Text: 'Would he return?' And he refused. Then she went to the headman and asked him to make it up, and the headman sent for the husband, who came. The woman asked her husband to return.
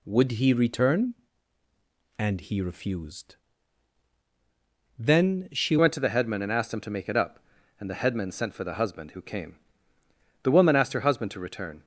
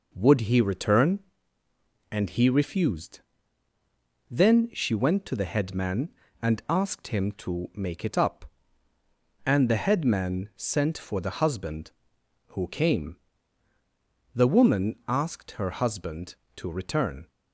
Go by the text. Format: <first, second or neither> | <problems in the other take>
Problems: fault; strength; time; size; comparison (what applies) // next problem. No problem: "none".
second | changes voice at "went"; from 5.7 s on; 6.1 s long